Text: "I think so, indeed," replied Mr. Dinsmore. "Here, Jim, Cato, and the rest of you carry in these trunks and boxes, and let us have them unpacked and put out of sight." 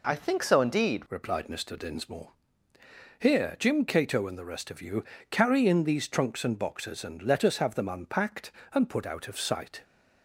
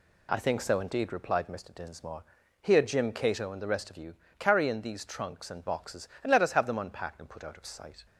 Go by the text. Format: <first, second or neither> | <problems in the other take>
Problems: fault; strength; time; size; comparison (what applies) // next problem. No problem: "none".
second | changes voice at "replied"; from 1.1 s on; 8.7 s long // pauses between "you" and "carry"; slight; at 5.0 s; 0.24 s long; slight in the second